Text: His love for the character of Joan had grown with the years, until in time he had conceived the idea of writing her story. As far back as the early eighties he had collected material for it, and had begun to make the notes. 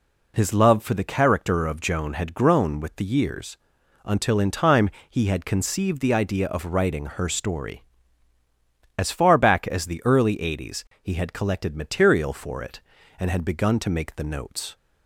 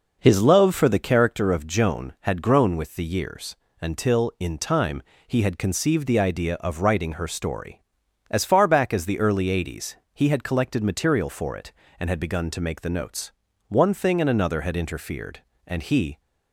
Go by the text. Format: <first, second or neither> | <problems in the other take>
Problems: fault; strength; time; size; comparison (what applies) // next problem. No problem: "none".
first | pauses between "time" and "he"; slight; at 5.0 s; 0.24 s long; slight in the first // pauses between "eighties" and "he"; slight; at 9.9 s; 0.18 s long; slight in the first // goes on to say "One thing and another had interfered and he"; strong; from 13.6 s on; 2.5 s long